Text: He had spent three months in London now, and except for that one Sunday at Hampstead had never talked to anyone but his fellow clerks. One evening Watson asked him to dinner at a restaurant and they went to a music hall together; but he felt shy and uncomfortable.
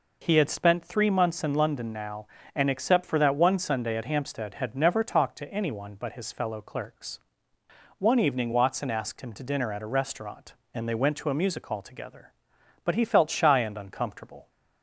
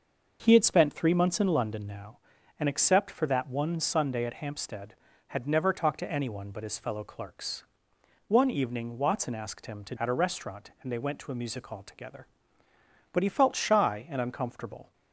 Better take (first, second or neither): first